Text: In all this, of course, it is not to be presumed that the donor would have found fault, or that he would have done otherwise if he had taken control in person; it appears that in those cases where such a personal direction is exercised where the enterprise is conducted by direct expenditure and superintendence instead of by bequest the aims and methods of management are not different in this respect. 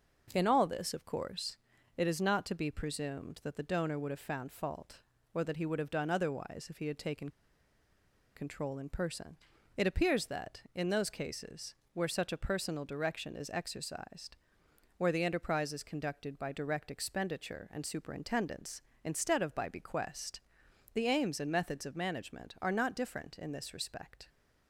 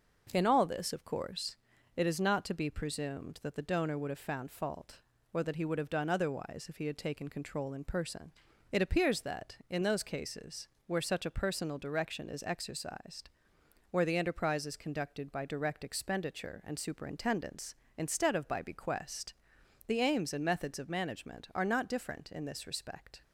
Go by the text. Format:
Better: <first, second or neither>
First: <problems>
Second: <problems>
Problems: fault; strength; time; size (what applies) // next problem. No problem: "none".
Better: second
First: pauses between "taken" and "control"; at 7.3 s; 1.0 s long // pauses between "cases" and "where"; slight; at 11.7 s; 0.20 s long // pauses between "exercised" and "where"; noticeable; at 14.3 s; 0.62 s long // pauses between "bequest" and "the"; noticeable; at 20.4 s; 0.52 s long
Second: pauses between "cases" and "where"; slight; at 10.6 s; 0.20 s long // pauses between "exercised" and "where"; noticeable; at 13.2 s; 0.62 s long // pauses between "bequest" and "the"; noticeable; at 19.3 s; 0.52 s long